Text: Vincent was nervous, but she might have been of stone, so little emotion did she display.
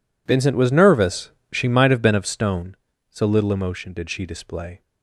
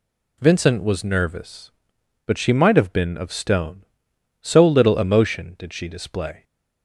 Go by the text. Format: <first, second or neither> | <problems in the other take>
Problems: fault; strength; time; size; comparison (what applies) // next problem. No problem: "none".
second | skips "but"; at 1.4 s